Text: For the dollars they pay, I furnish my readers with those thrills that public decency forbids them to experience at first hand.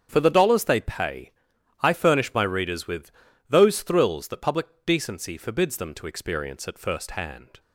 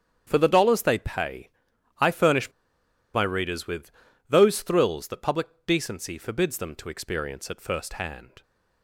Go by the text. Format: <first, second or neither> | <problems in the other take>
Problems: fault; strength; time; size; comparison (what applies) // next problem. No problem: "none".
first | starts louder than the rest; strong; until 1.2 s; 8 dB; strong in the first // pauses between "furnish" and "my"; noticeable; at 2.5 s; 0.62 s long // pauses between "with" and "those"; slight; at 3.9 s; 0.36 s long; slight in the first // pauses between "public" and "decency"; slight; at 5.4 s; 0.22 s long; slight in the first